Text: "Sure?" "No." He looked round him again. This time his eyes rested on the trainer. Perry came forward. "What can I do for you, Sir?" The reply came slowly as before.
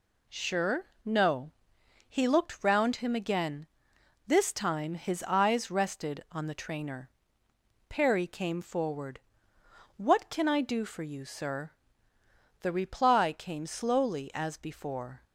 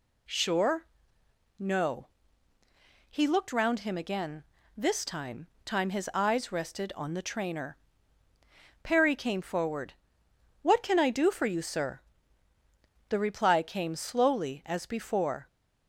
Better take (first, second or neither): first